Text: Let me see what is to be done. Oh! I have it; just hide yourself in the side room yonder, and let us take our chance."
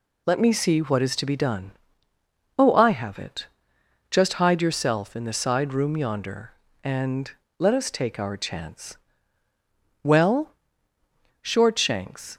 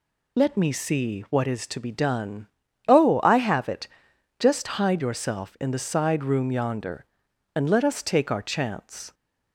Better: second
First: pauses between "and" and "let"; slight; at 7.2 s; 0.28 s long // goes on to say "Well Shortshanks"; strong; from 10.0 s on; 2.3 s long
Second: none

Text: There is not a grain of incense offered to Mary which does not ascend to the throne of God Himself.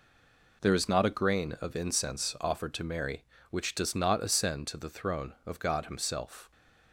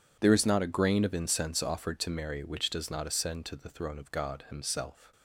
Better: second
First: stays silent before the first word; slight; until 0.6 s; 0.6 s long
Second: none

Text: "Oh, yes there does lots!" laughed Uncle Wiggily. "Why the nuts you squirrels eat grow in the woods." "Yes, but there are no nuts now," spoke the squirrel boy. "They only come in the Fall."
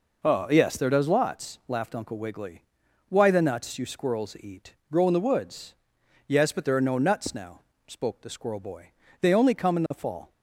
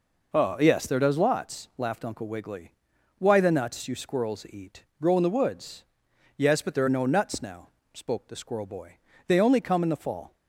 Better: neither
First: pauses between "eat" and "grow"; slight; at 4.7 s; 0.16 s long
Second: pauses between "eat" and "grow"; slight; at 4.8 s; 0.16 s long

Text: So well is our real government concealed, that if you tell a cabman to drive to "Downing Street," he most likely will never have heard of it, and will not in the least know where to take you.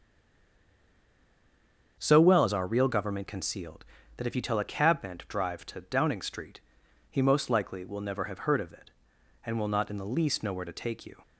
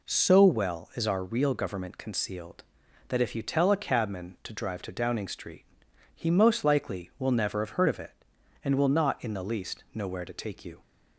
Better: second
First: stays silent before the first word; noticeable; until 1.9 s; 1.9 s long // starts louder than the rest; strong; until 2.9 s; 7 dB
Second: none

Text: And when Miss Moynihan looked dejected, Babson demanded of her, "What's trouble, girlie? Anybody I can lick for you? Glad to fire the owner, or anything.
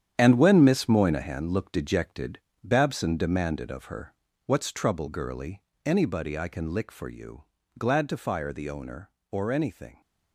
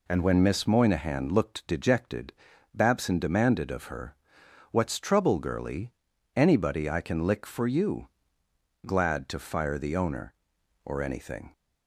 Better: second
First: gets quieter; strong; throughout; 10 dB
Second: none

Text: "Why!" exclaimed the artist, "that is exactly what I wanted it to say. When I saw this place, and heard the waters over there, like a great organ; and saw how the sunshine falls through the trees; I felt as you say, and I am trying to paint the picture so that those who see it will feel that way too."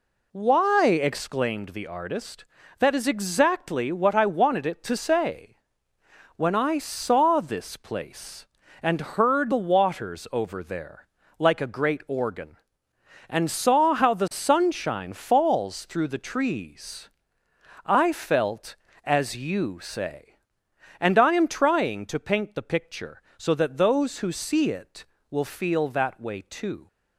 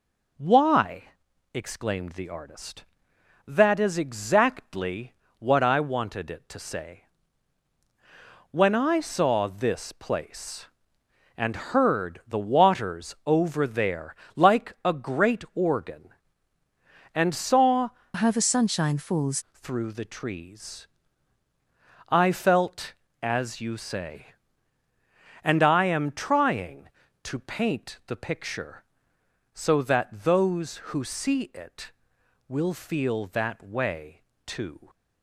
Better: first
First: none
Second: pauses between "exactly" and "what"; slight; at 5.1 s; 0.24 s long // changes voice from "how" to "falls"; from 18.1 to 19.3 s; 1.2 s long // pauses between "way" and "too"; slight; at 34.1 s; 0.24 s long

